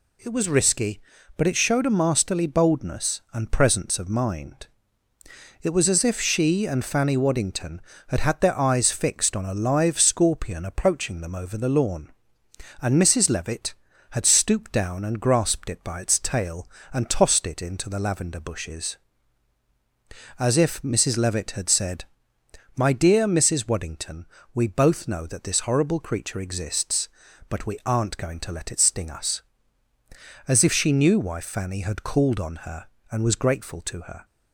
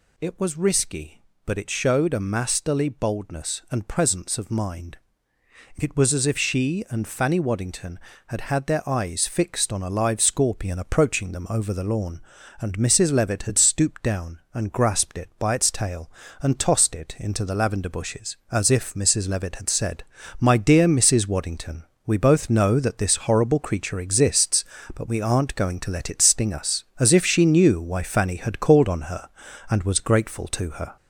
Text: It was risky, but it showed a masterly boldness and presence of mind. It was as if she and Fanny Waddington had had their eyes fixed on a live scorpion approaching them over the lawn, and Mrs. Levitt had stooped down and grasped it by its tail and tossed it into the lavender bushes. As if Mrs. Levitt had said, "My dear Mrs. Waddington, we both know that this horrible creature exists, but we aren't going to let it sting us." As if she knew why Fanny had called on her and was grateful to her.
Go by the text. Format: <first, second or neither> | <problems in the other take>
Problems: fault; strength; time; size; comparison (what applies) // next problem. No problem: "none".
first | gets louder; noticeable; throughout; 4.5 dB